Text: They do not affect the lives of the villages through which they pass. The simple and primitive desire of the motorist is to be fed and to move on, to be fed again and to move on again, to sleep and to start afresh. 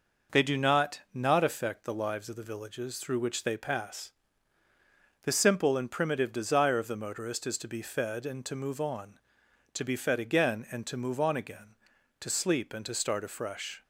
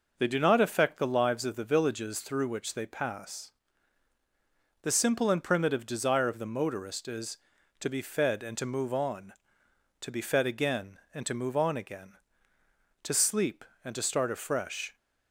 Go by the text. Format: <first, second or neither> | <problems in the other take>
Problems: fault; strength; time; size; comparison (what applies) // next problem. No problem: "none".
second | says "not" twice; at 1.1 s